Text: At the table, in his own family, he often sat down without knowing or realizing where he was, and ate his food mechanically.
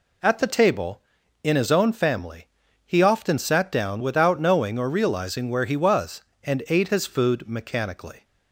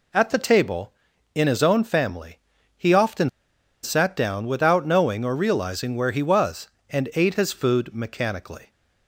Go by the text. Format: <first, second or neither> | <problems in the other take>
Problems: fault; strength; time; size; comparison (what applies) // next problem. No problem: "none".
first | pauses between "often" and "sat"; noticeable; at 3.2 s; 0.53 s long